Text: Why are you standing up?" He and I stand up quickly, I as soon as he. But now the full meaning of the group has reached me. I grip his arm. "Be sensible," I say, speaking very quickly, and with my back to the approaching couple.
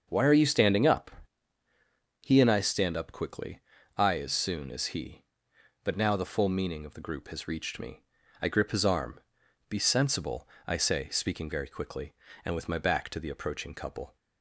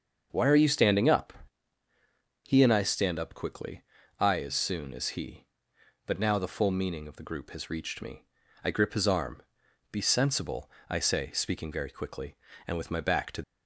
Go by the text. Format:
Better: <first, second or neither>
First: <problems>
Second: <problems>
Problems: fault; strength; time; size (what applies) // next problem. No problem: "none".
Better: first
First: starts louder than the rest; until 1.1 s; 6.5 dB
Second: starts louder than the rest; until 1.3 s; 6.5 dB // stops before "the approaching couple"; at 13.4 s